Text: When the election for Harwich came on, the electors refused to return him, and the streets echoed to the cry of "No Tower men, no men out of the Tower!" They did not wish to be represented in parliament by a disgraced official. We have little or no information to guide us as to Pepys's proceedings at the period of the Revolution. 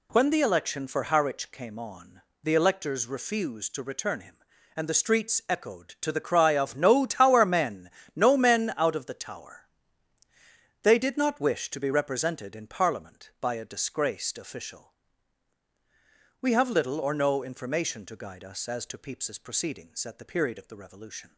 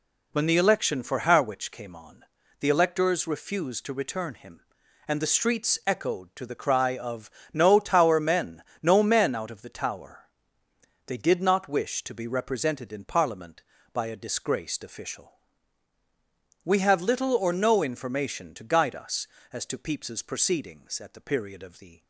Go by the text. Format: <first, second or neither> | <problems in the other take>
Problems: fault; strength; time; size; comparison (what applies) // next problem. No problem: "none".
first | pauses between "of" and "No"; slight; at 7.3 s; 0.22 s long // stops before "Revolution"; at 22.0 s